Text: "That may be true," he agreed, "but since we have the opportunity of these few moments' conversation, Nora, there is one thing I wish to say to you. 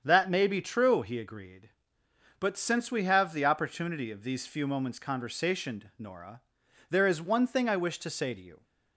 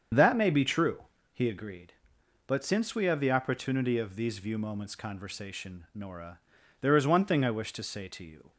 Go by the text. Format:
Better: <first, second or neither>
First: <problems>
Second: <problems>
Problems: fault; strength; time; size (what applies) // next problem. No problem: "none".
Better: first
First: starts louder than the rest; strong; until 1.0 s; 7.5 dB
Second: starts louder than the rest; strong; until 1.4 s; 7.5 dB // says "view" for "few"; at 4.3 s